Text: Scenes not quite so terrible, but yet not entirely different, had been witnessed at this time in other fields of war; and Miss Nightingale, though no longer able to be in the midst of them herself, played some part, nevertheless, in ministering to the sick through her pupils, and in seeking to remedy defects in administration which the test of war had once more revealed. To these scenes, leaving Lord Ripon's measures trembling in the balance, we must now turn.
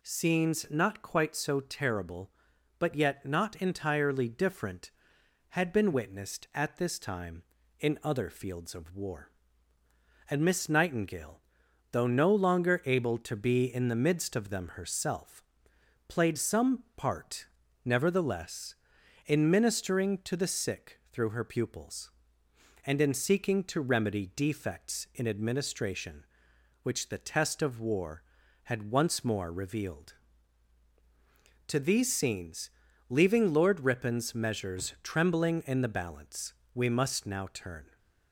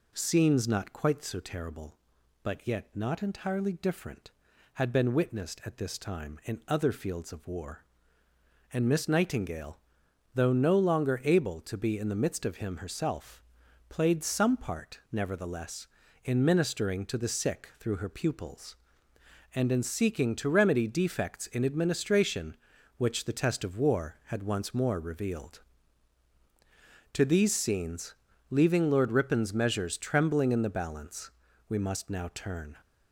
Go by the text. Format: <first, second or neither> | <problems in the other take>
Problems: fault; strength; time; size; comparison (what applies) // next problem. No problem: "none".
first | says "him" for "them"; at 12.5 s